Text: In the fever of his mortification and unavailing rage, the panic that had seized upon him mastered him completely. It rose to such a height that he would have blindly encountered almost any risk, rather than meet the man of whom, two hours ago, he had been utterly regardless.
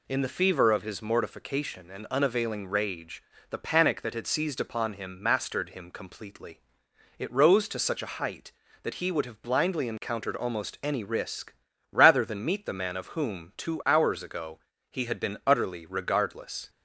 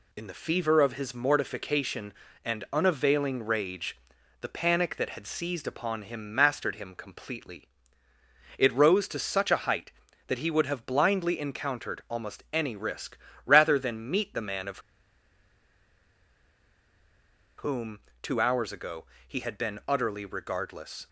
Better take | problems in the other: first | pauses between "of" and "whom"; strong; at 14.7 s; 2.7 s long

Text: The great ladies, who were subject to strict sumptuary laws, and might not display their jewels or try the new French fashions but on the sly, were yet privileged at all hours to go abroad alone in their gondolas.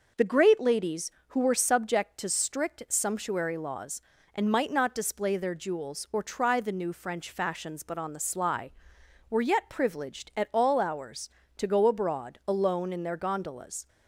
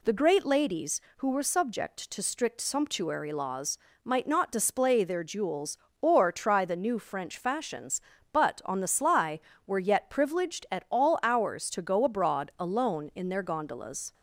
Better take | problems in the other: first | skips "and"; at 3.9 s

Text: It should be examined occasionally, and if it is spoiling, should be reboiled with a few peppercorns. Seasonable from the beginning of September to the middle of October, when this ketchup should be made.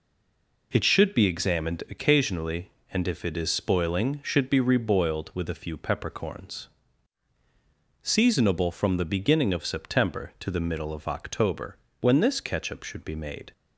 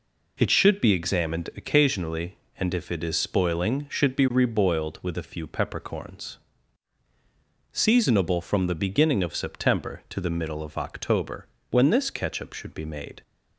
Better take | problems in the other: second | stays silent before the first word; slight; until 0.7 s; 0.7 s long

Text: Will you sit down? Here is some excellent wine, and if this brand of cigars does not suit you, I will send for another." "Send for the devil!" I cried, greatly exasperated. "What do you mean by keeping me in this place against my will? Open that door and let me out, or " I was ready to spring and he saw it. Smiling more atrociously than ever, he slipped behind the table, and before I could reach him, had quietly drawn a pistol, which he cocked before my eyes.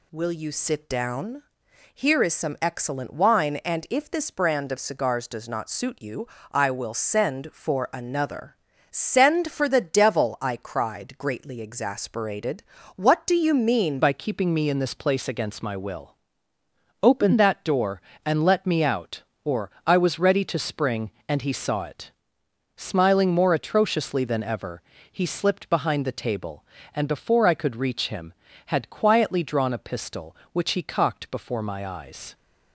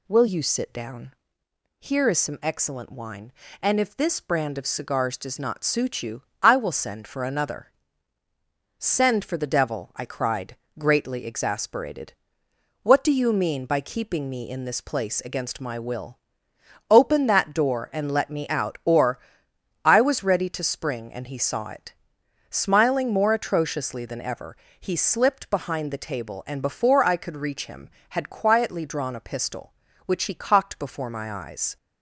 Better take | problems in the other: second | changes voice at "by"; from 14.0 s on; 18.3 s long

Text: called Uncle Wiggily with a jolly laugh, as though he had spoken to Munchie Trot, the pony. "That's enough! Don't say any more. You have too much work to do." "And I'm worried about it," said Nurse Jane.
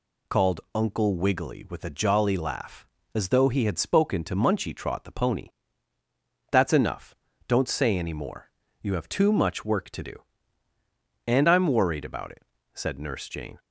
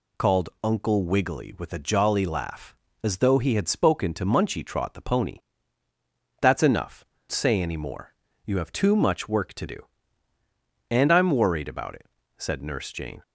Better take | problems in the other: first | skips "Don't"; at 7.1 s

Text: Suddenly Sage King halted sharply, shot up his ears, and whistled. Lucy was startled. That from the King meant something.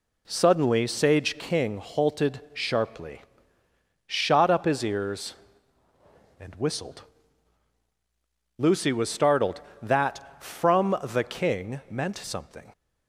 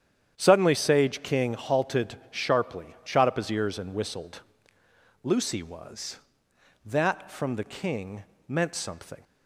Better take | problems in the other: first | starts louder than the rest; strong; until 1.3 s; 9 dB // pauses between "halted" and "sharply"; slight; at 2.1 s; 0.16 s long // skips "startled"; at 6.5 s // pauses between "King" and "meant"; slight; at 8.2 s; 0.24 s long

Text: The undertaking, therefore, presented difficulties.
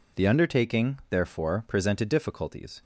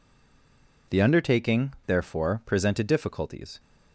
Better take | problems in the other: first | stays silent before the first word; slight; until 0.8 s; 0.8 s long

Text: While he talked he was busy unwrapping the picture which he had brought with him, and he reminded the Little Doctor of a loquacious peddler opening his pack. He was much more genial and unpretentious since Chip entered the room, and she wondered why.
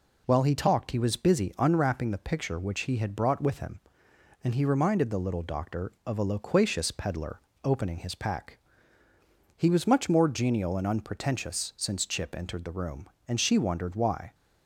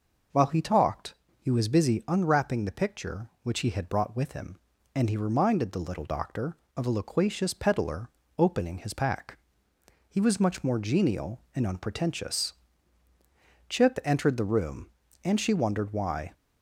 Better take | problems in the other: first | pauses between "talked" and "he"; slight; at 1.1 s; 0.26 s long // pauses between "peddler" and "opening"; slight; at 8.0 s; 0.30 s long; slight in the first // skips "since"; at 13.1 s

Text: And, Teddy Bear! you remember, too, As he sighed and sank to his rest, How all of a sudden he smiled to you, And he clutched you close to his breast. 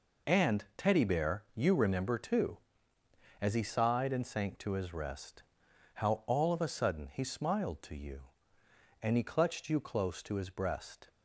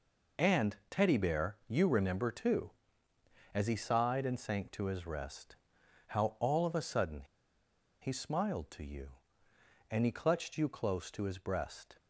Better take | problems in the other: first | pauses between "sudden" and "he"; noticeable; at 7.2 s; 0.79 s long

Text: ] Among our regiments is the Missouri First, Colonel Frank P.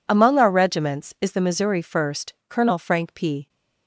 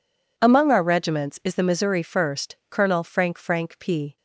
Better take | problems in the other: first | says "Frank" twice; at 3.3 s

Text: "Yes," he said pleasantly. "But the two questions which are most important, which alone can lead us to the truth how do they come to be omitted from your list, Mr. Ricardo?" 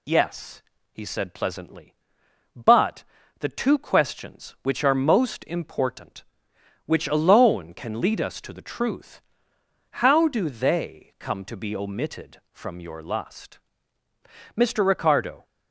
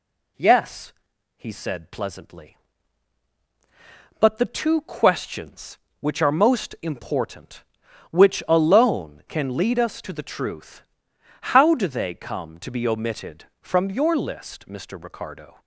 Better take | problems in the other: second | pauses between "But" and "the"; slight; at 3.0 s; 0.36 s long // pauses between "truth" and "how"; noticeable; at 9.2 s; 0.80 s long; noticeable in the second // says "lust" for "list"; at 13.0 s

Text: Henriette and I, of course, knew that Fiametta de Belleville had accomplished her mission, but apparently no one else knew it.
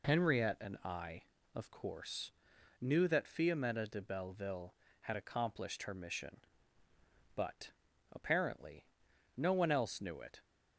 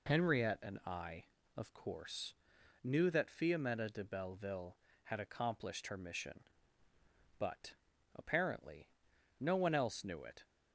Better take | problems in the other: neither | pauses between "but" and "apparently"; the same in both // pauses between "apparently" and "no"; noticeable; the same in both

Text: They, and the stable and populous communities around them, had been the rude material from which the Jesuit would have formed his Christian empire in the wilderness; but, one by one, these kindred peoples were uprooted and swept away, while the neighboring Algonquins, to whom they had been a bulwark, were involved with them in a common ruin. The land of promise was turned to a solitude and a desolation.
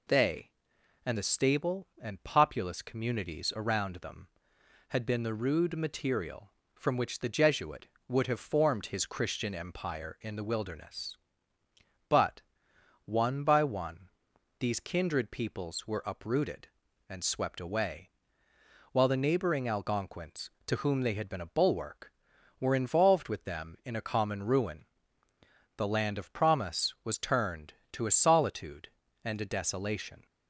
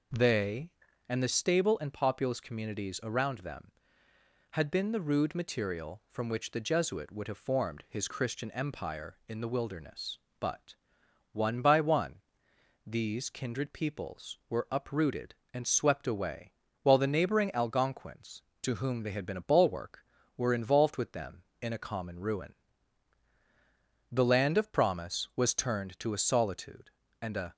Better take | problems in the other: first | stops before "desolation"; at 27.5 s

